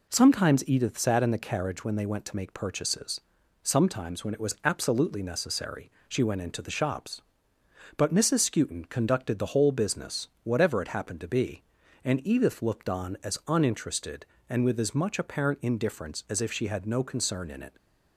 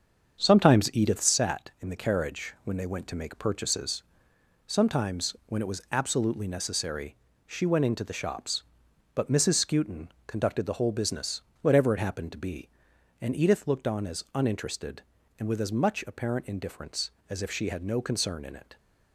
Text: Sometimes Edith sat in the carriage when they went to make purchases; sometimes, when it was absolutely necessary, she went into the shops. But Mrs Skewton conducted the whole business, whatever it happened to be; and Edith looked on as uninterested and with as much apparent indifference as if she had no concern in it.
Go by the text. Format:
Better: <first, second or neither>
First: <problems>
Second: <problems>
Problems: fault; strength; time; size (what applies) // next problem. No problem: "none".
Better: first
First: none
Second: starts louder than the rest; strong; until 1.3 s; 7 dB // pauses between "Skewton" and "conducted"; slight; at 10.0 s; 0.20 s long